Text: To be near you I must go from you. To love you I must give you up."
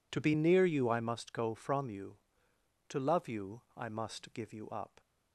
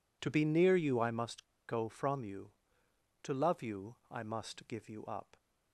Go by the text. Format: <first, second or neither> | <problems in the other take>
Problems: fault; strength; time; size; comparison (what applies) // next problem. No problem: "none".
first | pauses between "must" and "go"; slight; at 1.4 s; 0.23 s long // pauses between "you" and "I"; slight; at 3.9 s; 0.16 s long; slight in the first